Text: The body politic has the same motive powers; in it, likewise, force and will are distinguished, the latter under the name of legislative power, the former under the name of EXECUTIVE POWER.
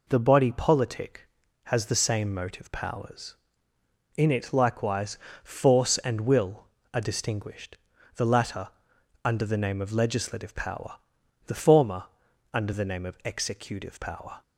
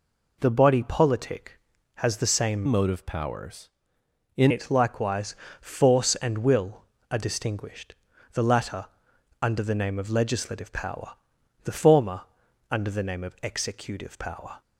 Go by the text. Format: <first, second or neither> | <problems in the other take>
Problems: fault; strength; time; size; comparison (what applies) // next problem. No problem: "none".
first | changes voice from "motive" to "in"; from 2.6 to 4.5 s; 1.9 s long // pauses between "latter" and "under"; noticeable; at 8.8 s; 0.56 s long; noticeable in the first // pauses between "former" and "under"; noticeable; at 12.2 s; 0.48 s long; noticeable in the first